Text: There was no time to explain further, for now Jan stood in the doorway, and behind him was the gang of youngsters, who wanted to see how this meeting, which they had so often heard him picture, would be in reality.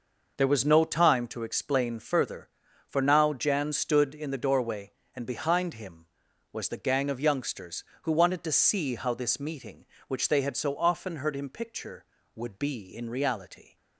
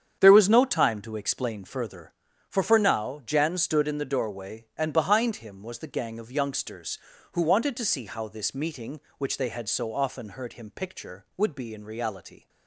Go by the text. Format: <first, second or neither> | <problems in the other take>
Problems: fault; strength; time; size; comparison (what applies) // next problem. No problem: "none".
first | starts louder than the rest; strong; until 1.2 s; 8 dB // says "for" twice; at 2.6 s